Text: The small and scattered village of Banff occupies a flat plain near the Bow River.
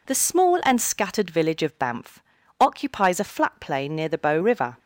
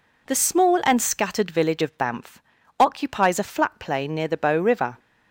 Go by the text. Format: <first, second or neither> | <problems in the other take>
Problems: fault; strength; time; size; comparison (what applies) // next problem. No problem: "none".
neither | pauses between "Banff" and "occupies"; slight; the same in both